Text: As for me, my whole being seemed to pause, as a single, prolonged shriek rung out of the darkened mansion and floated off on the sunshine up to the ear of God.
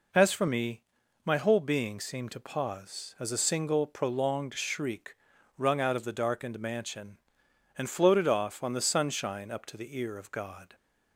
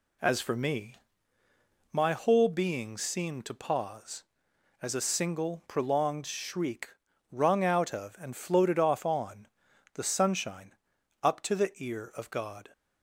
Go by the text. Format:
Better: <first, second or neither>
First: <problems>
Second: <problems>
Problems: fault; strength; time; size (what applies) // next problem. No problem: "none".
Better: first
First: pauses between "shriek" and "rung"; at 5.1 s; 0.44 s long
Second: pauses between "shriek" and "rung"; at 6.9 s; 0.40 s long // skips "the darkened mansion"; at 8.1 s // pauses between "on" and "the"; noticeable; at 9.4 s; 0.48 s long // pauses between "sunshine" and "up"; noticeable; at 10.7 s; 0.48 s long